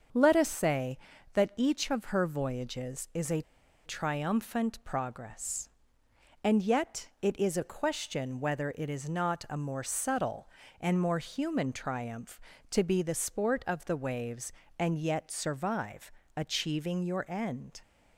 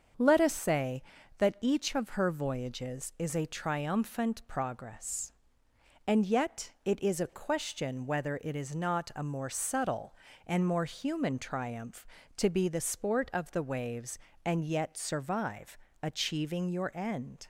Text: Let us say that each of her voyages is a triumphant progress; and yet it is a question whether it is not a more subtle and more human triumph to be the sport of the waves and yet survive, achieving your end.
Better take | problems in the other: second | starts louder than the rest; until 1.5 s; 7 dB; also in the second // pauses between "a" and "triumphant"; at 3.4 s; 0.44 s long

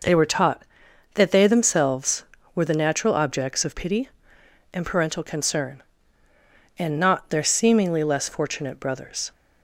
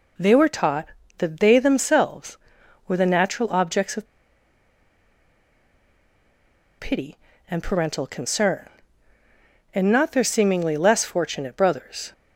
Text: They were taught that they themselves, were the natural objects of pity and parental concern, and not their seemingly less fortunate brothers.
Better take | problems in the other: first | pauses between "of" and "pity"; strong; at 4.0 s; 2.7 s long

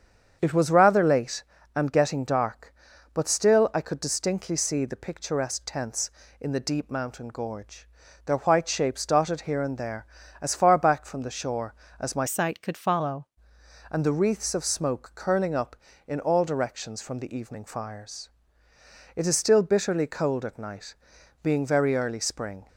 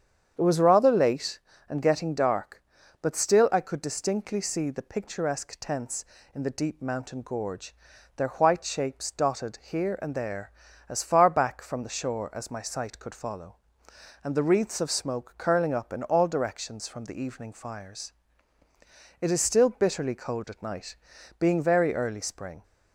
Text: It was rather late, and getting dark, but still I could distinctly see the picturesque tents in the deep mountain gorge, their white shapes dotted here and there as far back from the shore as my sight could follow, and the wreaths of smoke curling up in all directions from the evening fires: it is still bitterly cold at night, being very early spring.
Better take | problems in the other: second | starts louder than the rest; strong; until 1.4 s; 7.5 dB; strong in the second // changes voice from "sight" to "follow"; from 12.2 to 13.2 s; 1.0 s long

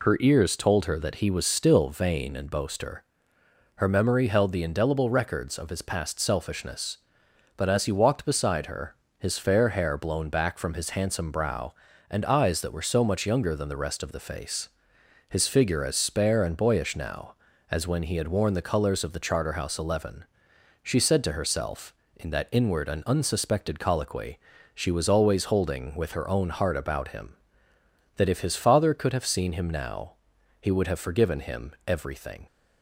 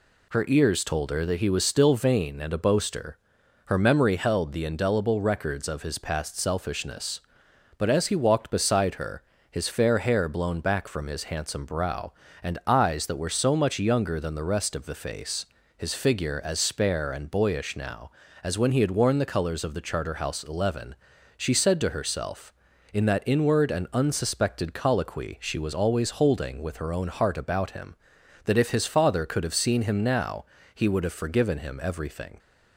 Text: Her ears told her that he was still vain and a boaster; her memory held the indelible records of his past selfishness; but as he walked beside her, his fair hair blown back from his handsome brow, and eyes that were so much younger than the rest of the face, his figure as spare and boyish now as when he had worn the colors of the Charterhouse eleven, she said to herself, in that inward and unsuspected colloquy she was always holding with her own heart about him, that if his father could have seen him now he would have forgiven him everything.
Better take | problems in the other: second | skips "a"; at 2.4 s // pauses between "colloquy" and "she"; slight; at 24.3 s; 0.34 s long // pauses between "now" and "he"; noticeable; at 30.1 s; 0.48 s long; slight in the second // pauses between "him" and "everything"; slight; at 31.7 s; 0.16 s long

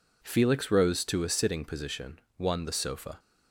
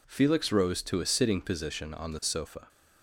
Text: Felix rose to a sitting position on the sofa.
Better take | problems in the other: second | says "one" for "on"; at 2.3 s

